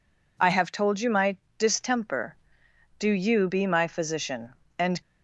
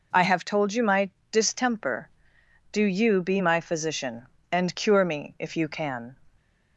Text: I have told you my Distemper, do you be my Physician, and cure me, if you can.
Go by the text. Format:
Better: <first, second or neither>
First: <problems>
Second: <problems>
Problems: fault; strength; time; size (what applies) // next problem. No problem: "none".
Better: second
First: pauses between "my" and "Distemper"; slight; at 1.3 s; 0.22 s long // stops before "cure me if you can"; at 5.0 s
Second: pauses between "my" and "Distemper"; slight; at 1.0 s; 0.22 s long